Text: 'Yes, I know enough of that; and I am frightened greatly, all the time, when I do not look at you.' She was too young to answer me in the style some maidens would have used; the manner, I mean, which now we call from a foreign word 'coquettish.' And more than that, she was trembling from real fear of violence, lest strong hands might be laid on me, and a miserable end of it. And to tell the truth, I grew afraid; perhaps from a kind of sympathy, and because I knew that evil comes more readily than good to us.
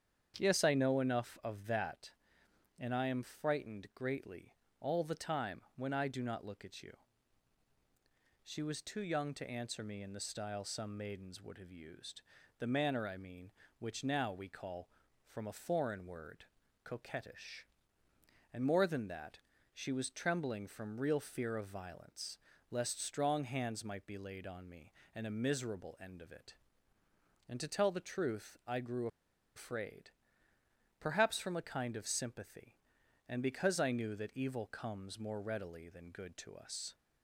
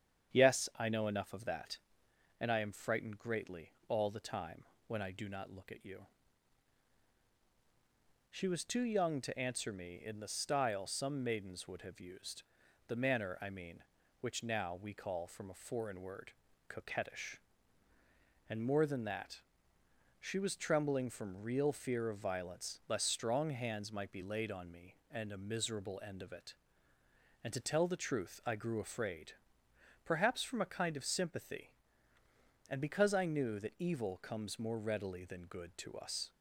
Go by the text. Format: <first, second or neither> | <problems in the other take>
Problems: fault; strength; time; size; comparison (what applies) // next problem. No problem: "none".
second | starts louder than the rest; strong; until 1.3 s; 8 dB; strong in the second // pauses between "word" and "coquettish"; at 16.4 s; 0.38 s long; also in the second // pauses between "grew" and "afraid"; noticeable; at 29.0 s; 0.48 s long